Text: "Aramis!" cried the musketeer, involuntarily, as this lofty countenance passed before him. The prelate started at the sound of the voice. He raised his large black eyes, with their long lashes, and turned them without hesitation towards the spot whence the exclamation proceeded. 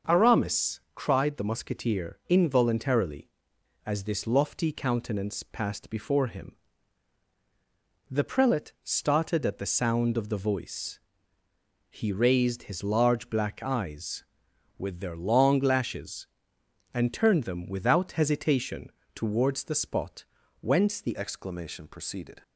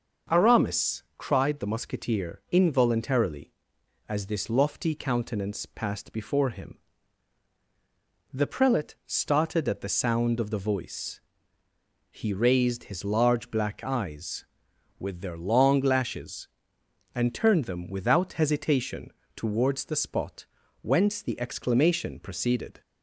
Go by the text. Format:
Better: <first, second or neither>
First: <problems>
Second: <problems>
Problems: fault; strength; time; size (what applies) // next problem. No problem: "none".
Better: second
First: starts louder than the rest; until 1.2 s; 6.5 dB // pauses between "hesitation" and "towards"; slight; at 18.9 s; 0.24 s long // pauses between "spot" and "whence"; slight; at 20.2 s; 0.36 s long // changes voice at "exclamation"; from 21.1 s on; 1.3 s long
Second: starts louder than the rest; until 1.4 s; 6.5 dB // pauses between "hesitation" and "towards"; slight; at 19.1 s; 0.24 s long // pauses between "spot" and "whence"; slight; at 20.4 s; 0.36 s long